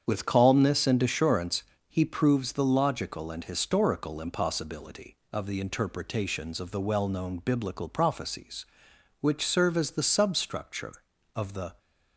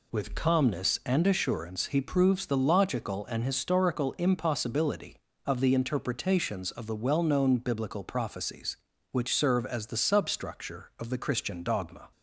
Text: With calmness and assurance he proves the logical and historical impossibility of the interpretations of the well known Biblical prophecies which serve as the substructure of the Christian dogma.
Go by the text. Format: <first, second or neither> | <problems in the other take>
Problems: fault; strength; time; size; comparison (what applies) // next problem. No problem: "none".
second | starts louder than the rest; strong; until 1.0 s; 8 dB // pauses between "assurance" and "he"; slight; at 1.6 s; 0.26 s long // stops before "Christian dogma"; at 11.7 s